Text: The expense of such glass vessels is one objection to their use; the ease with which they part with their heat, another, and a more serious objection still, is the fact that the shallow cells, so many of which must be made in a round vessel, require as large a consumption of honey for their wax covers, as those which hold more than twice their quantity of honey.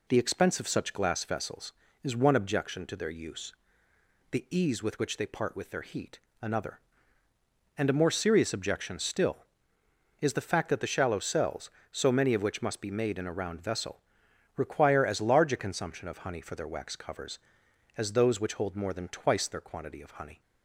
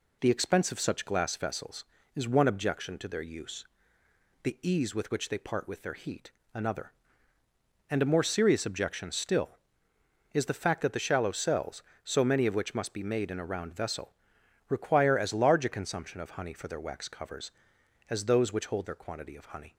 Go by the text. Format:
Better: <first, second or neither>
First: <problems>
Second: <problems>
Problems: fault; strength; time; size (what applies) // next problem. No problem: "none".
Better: first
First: none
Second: skips "more than twice"; at 18.8 s